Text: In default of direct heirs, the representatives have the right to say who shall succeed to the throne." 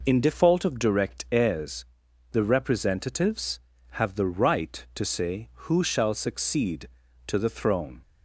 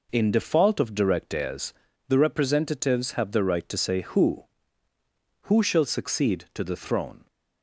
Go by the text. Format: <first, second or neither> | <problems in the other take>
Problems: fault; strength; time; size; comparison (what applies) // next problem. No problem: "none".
first | says "who" twice; at 5.4 s